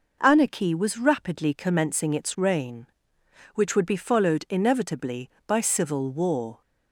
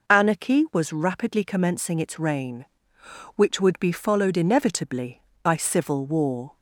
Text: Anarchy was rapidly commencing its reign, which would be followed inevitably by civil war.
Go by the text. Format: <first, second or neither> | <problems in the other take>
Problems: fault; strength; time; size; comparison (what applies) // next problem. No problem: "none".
neither | none